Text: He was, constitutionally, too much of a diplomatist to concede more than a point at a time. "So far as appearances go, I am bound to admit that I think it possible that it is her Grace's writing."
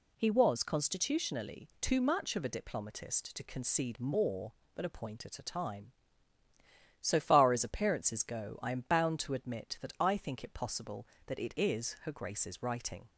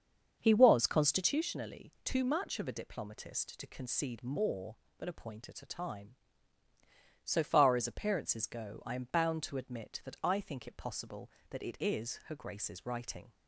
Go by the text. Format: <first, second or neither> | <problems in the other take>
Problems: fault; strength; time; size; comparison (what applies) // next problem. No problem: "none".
first | starts louder than the rest; until 1.5 s; 7 dB